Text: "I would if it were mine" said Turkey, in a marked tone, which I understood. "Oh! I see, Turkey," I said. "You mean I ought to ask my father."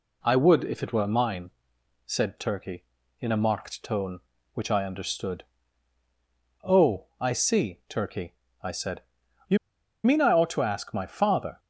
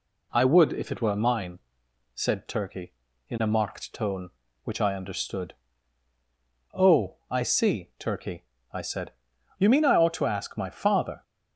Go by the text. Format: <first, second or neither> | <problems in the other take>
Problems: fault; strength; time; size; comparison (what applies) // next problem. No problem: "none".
second | pauses between "mine" and "said"; noticeable; at 1.4 s; 0.56 s long; noticeable in the second // pauses between "You" and "mean"; noticeable; at 9.5 s; 0.47 s long